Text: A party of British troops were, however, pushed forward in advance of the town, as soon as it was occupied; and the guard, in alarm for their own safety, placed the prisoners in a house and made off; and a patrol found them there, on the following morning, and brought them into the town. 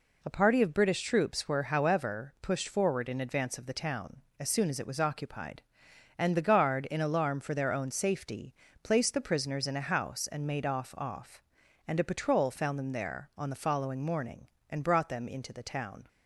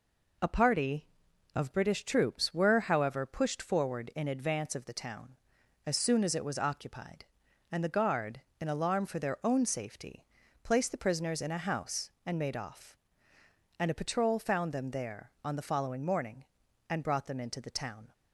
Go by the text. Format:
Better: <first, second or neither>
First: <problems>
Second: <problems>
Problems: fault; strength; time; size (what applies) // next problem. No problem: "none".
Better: second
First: says "off" twice; at 10.9 s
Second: none